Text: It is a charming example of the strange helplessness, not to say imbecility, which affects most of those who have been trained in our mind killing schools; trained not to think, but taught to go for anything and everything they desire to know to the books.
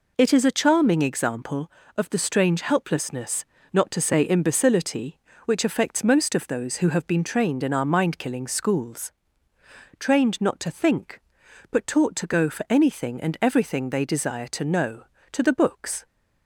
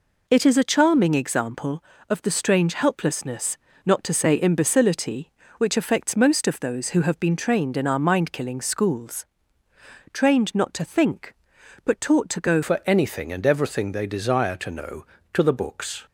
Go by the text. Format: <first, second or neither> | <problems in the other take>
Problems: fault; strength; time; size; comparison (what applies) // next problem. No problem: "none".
first | changes voice at "for"; from 12.6 s on; 3.4 s long